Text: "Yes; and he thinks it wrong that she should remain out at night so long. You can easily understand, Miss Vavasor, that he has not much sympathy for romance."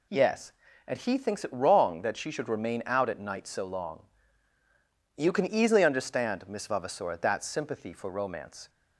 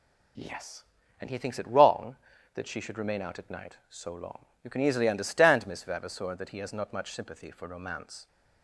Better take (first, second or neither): second